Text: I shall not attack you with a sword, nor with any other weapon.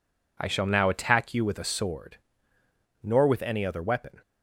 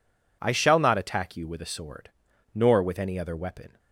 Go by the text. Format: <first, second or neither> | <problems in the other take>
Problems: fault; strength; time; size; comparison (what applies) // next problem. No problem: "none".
second | says "now" for "not"; at 0.6 s